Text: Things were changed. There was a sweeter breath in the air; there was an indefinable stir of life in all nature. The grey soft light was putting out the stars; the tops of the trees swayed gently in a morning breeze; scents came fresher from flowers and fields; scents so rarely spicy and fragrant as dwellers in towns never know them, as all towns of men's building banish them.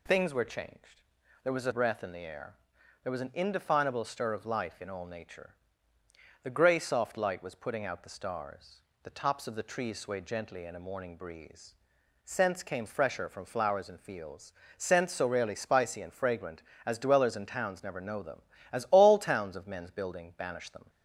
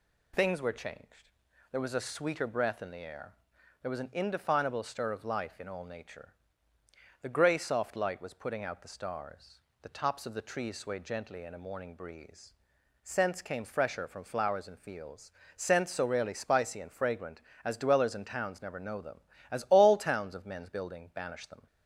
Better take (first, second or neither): second